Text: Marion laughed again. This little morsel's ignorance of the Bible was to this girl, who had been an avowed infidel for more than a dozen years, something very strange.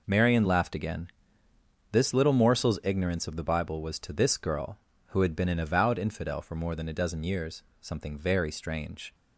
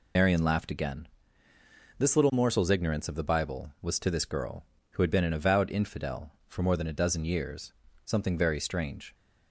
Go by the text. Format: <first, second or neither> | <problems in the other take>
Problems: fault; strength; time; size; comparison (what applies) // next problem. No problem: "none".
first | loses the start of "Marion"; at 0.1 s; 125 ms